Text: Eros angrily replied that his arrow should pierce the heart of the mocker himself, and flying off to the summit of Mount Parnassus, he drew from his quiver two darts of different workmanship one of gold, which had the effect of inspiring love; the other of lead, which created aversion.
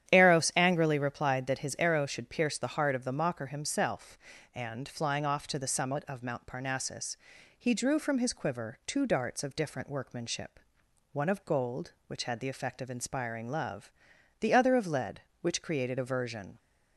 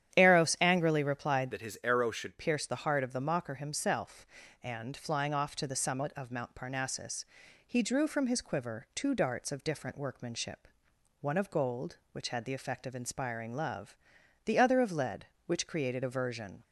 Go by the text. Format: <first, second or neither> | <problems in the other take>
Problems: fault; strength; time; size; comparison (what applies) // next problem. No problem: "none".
first | starts louder than the rest; strong; until 1.1 s; 10.5 dB; strong in the first // changes voice from "that" to "should"; from 1.5 to 2.3 s; 0.8 s long // pauses between "workmanship" and "one"; noticeable; at 10.6 s; 0.52 s long; noticeable in the first